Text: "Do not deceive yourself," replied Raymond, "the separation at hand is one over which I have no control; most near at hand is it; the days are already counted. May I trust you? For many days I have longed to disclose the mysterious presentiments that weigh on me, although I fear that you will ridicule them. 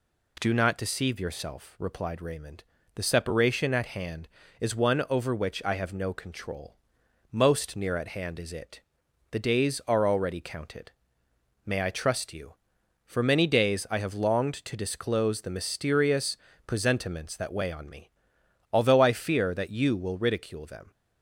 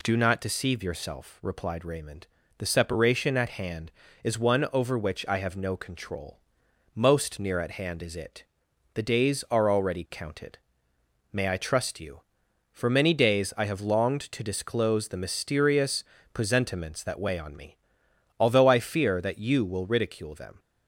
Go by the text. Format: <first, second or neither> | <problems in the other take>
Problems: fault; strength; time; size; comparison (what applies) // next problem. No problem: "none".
neither | pauses between "mysterious" and "presentiments"; slight; the same in both